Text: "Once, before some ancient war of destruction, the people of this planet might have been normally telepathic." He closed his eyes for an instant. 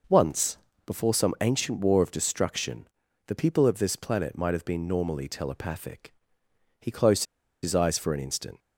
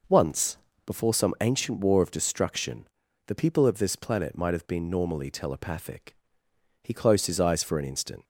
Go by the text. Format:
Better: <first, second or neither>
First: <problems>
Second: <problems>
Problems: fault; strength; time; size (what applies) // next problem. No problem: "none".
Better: second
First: pauses between "closed" and "his"; at 7.2 s; 0.39 s long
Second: none